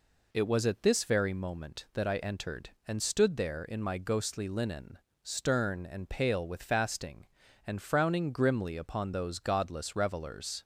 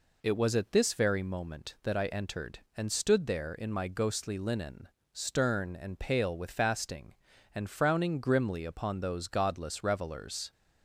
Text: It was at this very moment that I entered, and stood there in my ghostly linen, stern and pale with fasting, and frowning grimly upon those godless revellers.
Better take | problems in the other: neither | none

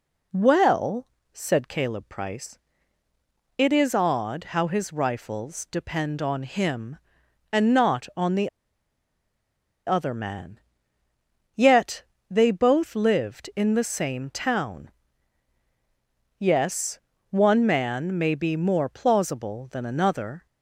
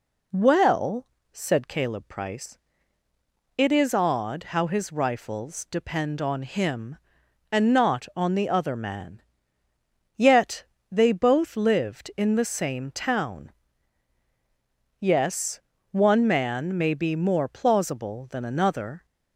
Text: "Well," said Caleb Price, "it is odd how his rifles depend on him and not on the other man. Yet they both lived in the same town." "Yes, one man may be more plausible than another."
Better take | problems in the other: second | pauses between "the" and "other"; strong; at 8.4 s; 1.3 s long // pauses between "Yet" and "they"; slight; at 12.0 s; 0.26 s long; slight in the second

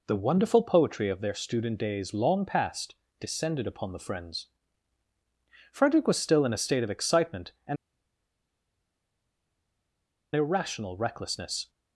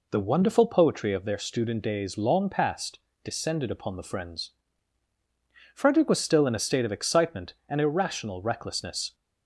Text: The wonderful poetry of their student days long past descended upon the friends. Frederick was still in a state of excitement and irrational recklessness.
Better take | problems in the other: second | pauses between "past" and "descended"; slight; at 2.9 s; 0.26 s long; slight in the second // pauses between "and" and "irrational"; strong; at 7.7 s; 2.5 s long

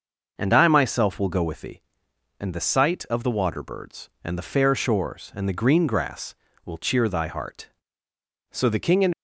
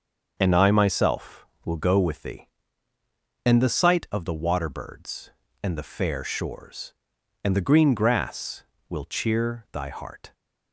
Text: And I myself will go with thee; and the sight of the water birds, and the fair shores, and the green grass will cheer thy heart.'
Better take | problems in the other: second | starts louder than the rest; until 1.3 s; 6 dB; also in the second // goes on to say "So the King and"; noticeable; from 8.4 s on; 0.66 s long

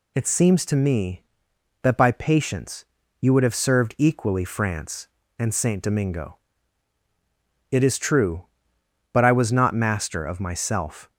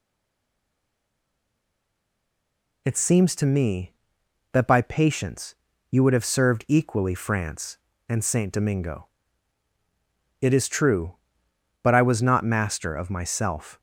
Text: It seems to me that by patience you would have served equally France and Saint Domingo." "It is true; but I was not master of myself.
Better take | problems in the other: first | stays silent before the first word; strong; until 2.8 s; 2.8 s long // pauses between "patience" and "you"; slight; at 5.5 s; 0.36 s long; slight in the first

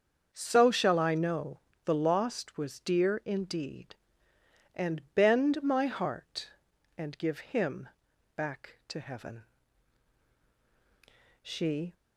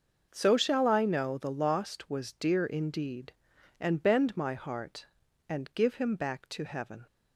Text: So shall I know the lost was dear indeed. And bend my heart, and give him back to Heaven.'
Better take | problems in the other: second | starts louder than the rest; until 1.3 s; 7 dB; noticeable in the second // pauses between "know" and "the"; slight; at 1.5 s; 0.24 s long // pauses between "him" and "back"; noticeable; at 7.8 s; 0.48 s long // goes on to say "She"; from 11.4 s on; 0.52 s long

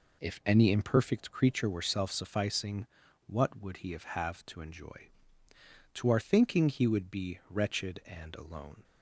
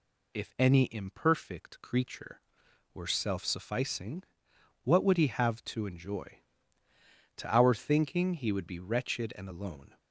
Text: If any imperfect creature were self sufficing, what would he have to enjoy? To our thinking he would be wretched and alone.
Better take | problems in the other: second | says "have" twice; at 4.0 s

